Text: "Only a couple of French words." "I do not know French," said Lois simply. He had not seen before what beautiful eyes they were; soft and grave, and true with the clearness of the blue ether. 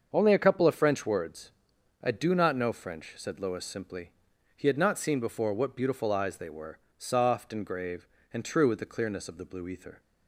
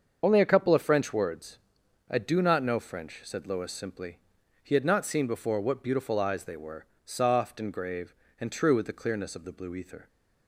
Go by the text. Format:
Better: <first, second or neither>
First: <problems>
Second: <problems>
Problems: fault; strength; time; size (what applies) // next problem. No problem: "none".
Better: first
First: starts louder than the rest; until 1.1 s; 6.5 dB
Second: loses the start of "Only"; at 0.2 s; 30 ms // starts louder than the rest; until 1.2 s; 6.5 dB